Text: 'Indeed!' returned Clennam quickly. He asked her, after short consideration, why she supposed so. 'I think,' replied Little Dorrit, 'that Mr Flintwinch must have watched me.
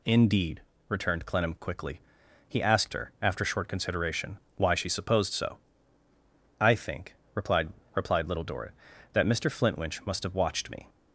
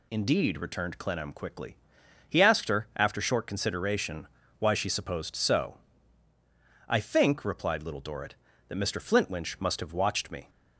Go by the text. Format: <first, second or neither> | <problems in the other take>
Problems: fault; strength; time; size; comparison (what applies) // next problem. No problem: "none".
second | says "replied" twice; at 7.9 s